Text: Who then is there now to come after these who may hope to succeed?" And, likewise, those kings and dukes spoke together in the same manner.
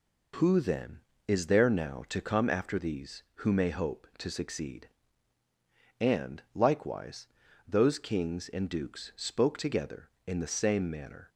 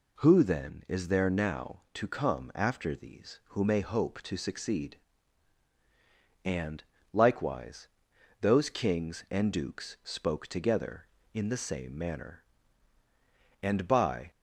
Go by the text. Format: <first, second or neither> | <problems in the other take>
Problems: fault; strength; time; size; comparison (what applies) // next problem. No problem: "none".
first | goes on to say "And by"; noticeable; from 13.6 s on; 0.70 s long